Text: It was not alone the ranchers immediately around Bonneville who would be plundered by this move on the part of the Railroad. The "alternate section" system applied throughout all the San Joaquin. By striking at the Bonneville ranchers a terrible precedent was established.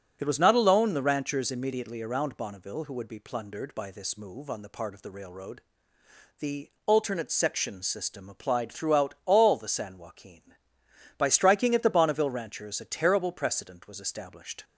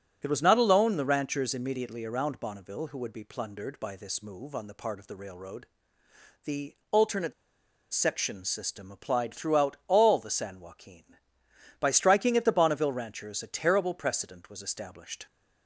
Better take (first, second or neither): first